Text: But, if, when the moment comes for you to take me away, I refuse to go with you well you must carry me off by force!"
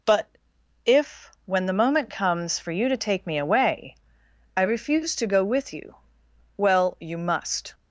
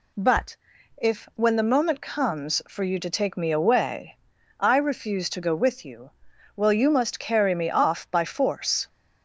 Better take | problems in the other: second | pauses between "you" and "well"; noticeable; at 5.9 s; 0.64 s long; also in the second // stops before "carry me off by force"; at 7.7 s

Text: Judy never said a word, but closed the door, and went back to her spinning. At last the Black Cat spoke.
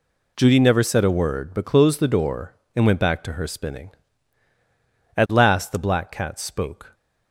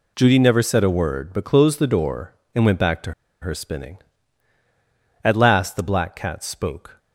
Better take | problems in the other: first | pauses between "to" and "her"; slight; at 3.1 s; 0.29 s long

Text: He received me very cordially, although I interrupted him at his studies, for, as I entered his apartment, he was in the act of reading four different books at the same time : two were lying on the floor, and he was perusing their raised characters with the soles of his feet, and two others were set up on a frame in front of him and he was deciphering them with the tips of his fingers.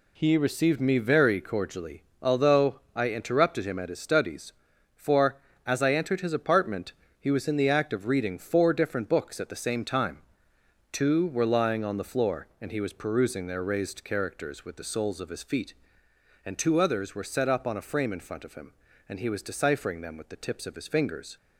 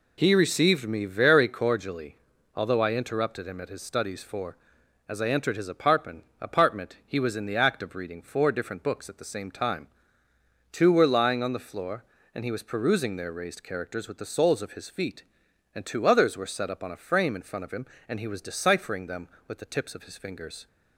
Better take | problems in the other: first | says "apartment" twice; at 6.4 s

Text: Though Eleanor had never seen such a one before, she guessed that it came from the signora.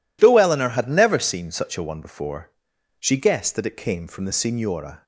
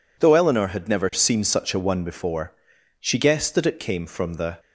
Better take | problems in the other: first | stops before "signora"; at 4.5 s

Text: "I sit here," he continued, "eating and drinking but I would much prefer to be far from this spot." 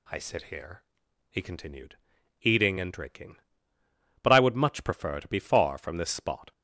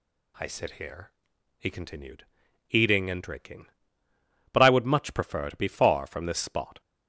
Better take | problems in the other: neither | none

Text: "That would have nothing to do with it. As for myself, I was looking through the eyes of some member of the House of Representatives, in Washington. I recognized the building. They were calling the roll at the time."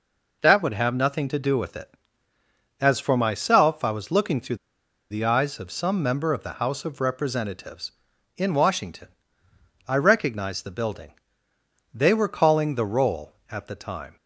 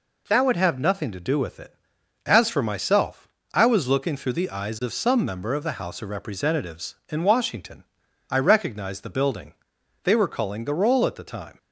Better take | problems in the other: second | pauses between "through" and "the"; noticeable; at 4.5 s; 0.53 s long

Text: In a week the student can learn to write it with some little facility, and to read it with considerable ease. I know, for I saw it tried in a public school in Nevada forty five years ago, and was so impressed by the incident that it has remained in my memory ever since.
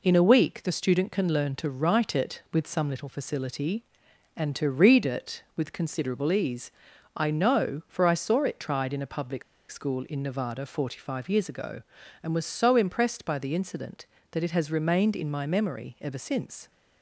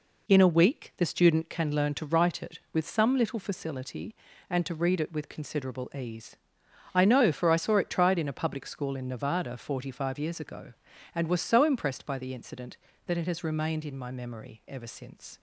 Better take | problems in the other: second | pauses between "public" and "school"; slight; at 9.4 s; 0.27 s long

